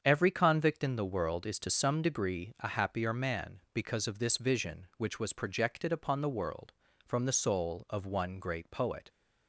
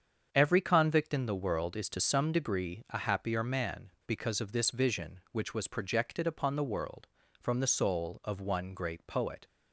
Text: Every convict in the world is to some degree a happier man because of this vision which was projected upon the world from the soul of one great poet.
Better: neither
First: starts louder than the rest; strong; until 1.0 s; 7.5 dB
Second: starts louder than the rest; strong; until 1.3 s; 7.5 dB

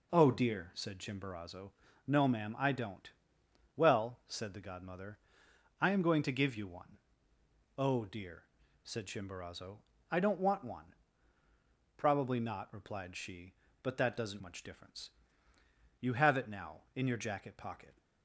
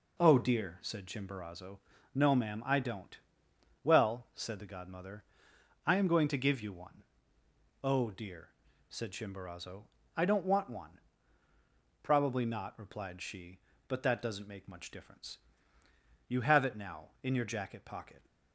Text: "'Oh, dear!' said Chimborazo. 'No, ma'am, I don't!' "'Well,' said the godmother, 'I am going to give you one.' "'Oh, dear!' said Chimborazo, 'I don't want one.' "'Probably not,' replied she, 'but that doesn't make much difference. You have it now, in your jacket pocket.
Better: second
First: skips "make"; at 14.4 s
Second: none

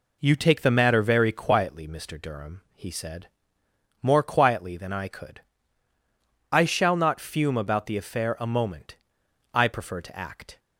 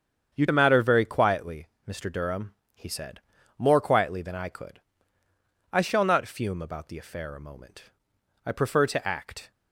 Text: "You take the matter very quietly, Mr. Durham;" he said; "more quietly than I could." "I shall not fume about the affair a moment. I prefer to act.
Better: first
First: none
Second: starts louder than the rest; strong; until 1.3 s; 7.5 dB // skips "take"; at 0.4 s

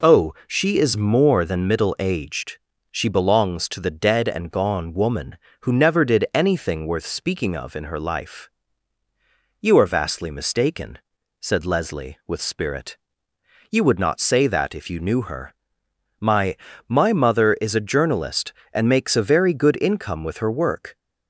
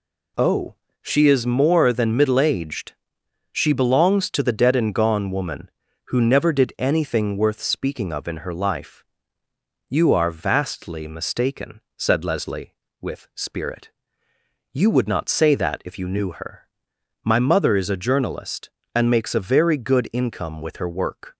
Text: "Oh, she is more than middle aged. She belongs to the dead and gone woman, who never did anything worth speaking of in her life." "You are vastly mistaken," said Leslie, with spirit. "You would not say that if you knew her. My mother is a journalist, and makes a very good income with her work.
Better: second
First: says "My" twice; at 16.8 s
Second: none

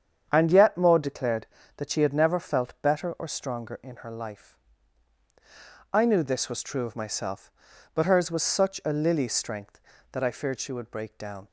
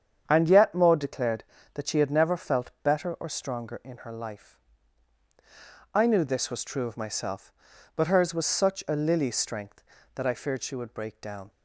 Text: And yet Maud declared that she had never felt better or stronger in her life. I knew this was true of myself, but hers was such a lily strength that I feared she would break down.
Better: neither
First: starts louder than the rest; strong; until 1.3 s; 8 dB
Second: starts louder than the rest; strong; until 1.2 s; 8 dB

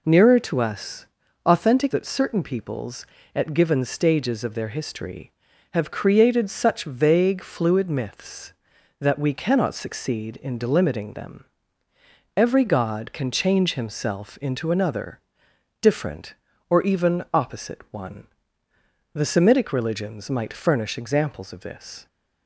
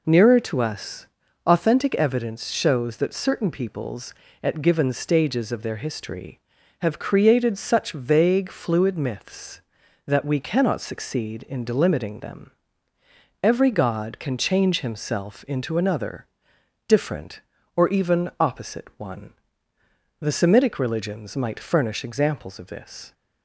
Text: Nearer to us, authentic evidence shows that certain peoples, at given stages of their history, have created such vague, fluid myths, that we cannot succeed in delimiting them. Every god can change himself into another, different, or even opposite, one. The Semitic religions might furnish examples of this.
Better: second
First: skips "evidence shows"; at 1.9 s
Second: none

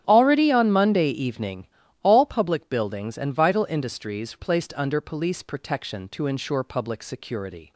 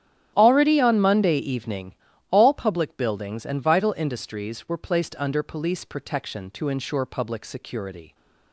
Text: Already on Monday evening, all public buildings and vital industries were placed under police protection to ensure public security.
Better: second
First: starts louder than the rest; strong; until 1.0 s; 10.5 dB // skips "were"; at 4.3 s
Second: starts louder than the rest; strong; until 1.3 s; 11 dB

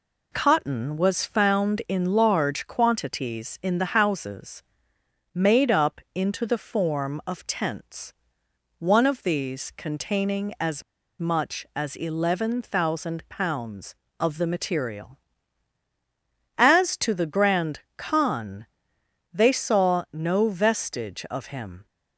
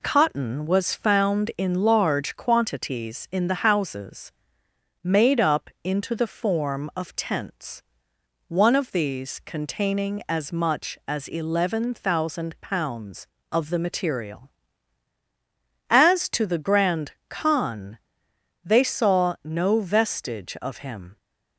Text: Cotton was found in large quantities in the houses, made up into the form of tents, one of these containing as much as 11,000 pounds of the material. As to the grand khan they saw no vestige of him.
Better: second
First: pauses between "as" and "much"; at 10.8 s; 0.36 s long // pauses between "grand" and "khan"; slight; at 17.7 s; 0.18 s long // pauses between "khan" and "they"; noticeable; at 18.6 s; 0.68 s long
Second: pauses between "grand" and "khan"; slight; at 17.1 s; 0.18 s long // pauses between "khan" and "they"; noticeable; at 17.9 s; 0.67 s long

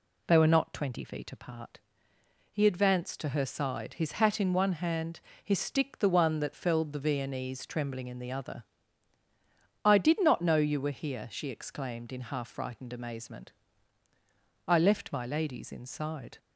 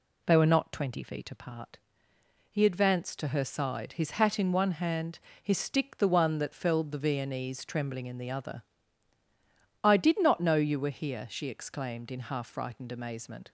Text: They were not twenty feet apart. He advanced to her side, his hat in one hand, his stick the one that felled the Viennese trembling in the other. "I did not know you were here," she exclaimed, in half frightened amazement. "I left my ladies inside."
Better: first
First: none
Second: stops before "I left my ladies inside"; at 13.4 s

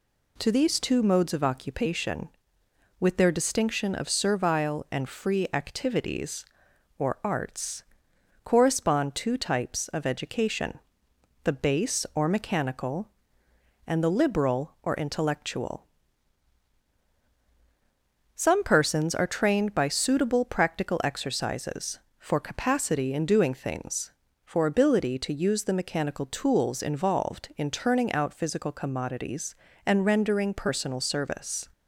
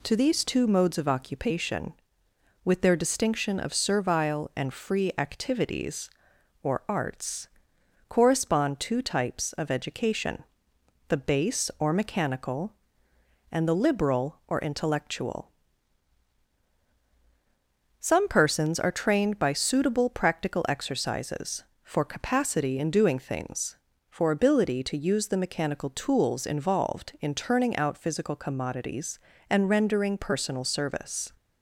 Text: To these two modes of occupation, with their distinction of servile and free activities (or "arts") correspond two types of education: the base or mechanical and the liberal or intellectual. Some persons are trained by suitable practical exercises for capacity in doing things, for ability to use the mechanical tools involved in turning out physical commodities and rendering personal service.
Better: neither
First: none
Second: none

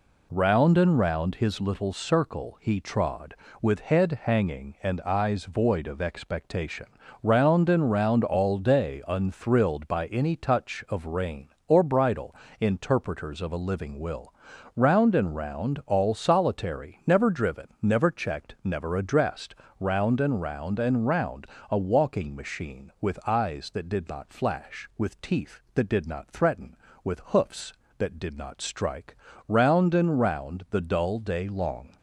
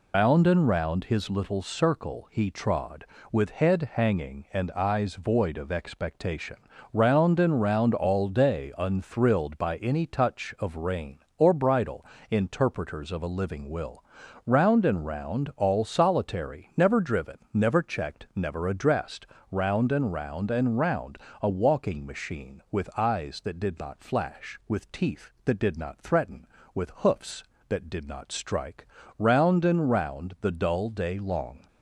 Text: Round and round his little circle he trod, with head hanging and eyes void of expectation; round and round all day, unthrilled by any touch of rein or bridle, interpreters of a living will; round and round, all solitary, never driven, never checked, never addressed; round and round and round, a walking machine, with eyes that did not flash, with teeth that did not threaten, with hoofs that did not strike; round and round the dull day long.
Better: first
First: none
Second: loses the start of "Round"; at 0.1 s; 145 ms

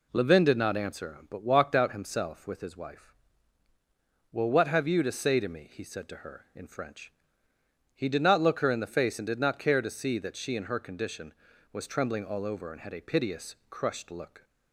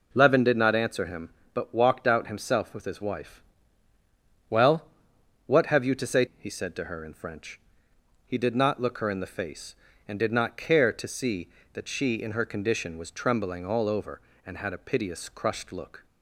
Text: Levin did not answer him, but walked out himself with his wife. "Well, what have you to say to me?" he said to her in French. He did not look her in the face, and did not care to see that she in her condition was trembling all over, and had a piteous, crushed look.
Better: first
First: none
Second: skips "to me"; at 6.3 s

